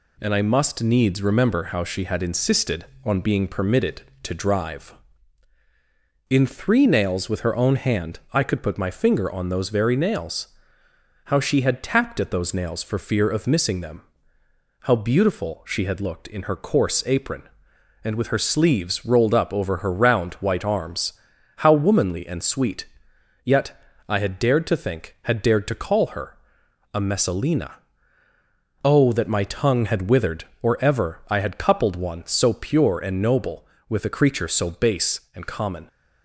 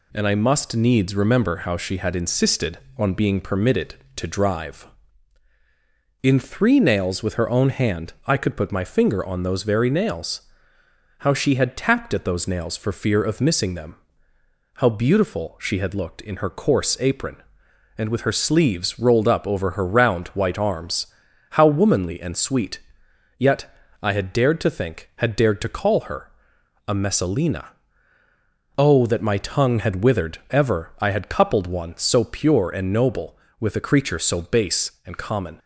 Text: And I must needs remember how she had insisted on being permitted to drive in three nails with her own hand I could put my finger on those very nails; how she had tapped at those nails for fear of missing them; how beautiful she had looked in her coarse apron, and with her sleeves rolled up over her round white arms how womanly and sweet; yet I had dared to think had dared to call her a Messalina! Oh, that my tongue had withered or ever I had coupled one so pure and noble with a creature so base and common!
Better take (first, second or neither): first